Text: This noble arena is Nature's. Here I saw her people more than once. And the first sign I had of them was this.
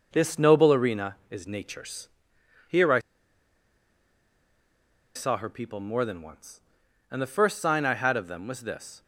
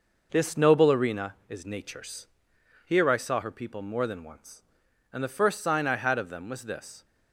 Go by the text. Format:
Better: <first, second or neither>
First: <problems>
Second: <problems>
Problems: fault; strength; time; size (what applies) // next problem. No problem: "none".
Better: second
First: pauses between "I" and "saw"; strong; at 2.9 s; 2.1 s long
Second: none